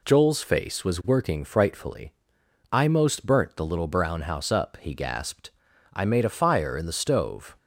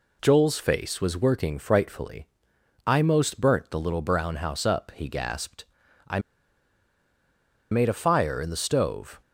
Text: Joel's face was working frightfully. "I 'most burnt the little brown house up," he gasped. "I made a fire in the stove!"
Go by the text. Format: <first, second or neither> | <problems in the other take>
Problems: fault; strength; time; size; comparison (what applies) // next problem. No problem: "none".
first | pauses between "I" and "made"; strong; at 6.1 s; 1.5 s long